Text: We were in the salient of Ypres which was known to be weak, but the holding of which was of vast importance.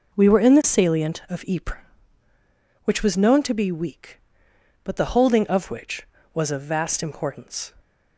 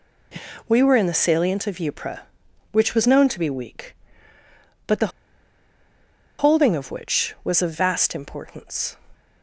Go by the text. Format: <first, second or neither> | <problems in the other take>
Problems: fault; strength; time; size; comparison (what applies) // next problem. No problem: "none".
first | pauses between "the" and "holding"; strong; at 5.1 s; 1.2 s long